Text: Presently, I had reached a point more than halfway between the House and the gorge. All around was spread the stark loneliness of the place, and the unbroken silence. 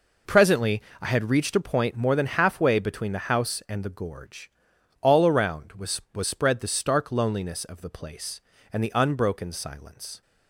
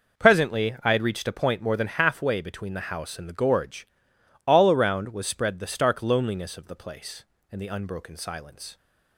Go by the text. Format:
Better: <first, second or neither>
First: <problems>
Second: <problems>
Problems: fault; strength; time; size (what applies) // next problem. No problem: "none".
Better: second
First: says "was" twice; at 6.1 s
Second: none